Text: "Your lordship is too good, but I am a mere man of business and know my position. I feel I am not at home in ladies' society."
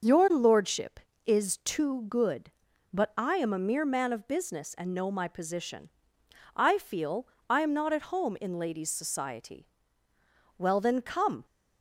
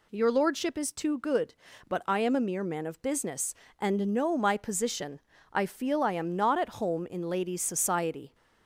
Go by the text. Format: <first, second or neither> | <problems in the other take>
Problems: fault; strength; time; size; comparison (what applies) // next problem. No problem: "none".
second | starts louder than the rest; noticeable; until 1.3 s; 6 dB // pauses between "feel" and "I"; slight; at 7.2 s; 0.22 s long // goes on to say "Well then come"; noticeable; from 10.5 s on; 0.86 s long